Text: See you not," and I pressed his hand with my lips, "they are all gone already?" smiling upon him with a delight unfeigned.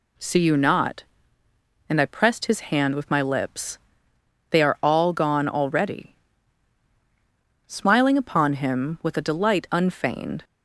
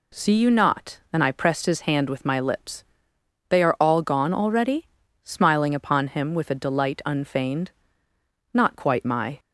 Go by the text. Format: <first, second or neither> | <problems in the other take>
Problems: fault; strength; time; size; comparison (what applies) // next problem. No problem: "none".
first | goes on to say "Not quite my"; noticeable; from 8.5 s on; 0.86 s long